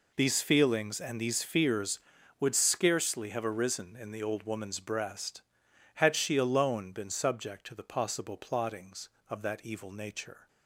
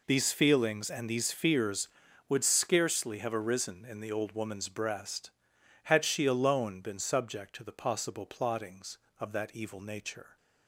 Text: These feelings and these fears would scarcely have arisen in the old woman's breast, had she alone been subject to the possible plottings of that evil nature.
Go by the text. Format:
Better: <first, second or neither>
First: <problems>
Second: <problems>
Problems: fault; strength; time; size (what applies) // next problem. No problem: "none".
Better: neither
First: none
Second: none